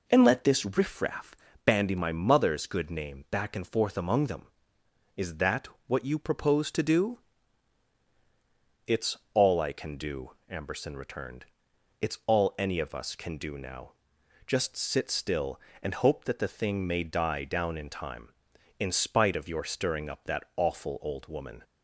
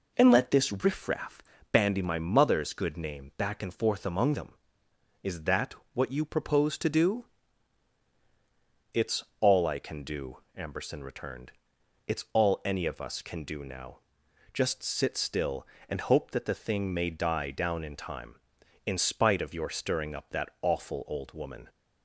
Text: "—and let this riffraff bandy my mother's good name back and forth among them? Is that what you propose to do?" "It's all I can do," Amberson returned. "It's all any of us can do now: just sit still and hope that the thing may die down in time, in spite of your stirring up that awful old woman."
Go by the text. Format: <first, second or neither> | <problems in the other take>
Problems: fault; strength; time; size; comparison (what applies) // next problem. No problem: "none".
neither | pauses between "riffraff" and "bandy"; slight; the same in both // pauses between "that" and "what"; slight; the same in both // pauses between "It's" and "all"; slight; the same in both